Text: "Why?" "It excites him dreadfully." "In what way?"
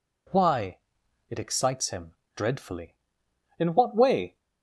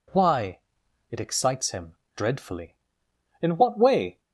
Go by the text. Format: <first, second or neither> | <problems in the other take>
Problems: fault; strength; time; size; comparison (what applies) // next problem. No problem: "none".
neither | pauses between "him" and "dreadfully"; slight; the same in both